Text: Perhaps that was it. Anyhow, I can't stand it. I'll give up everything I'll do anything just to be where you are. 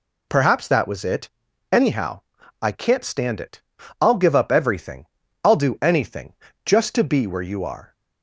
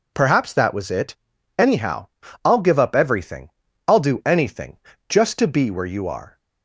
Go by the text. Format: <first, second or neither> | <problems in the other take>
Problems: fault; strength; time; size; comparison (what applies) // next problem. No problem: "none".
first | skips "I can't stand it"; at 2.2 s // pauses between "everything" and "I'll"; at 3.4 s; 0.38 s long; also in the first // pauses between "anything" and "just"; slight; at 4.7 s; 0.32 s long; slight in the first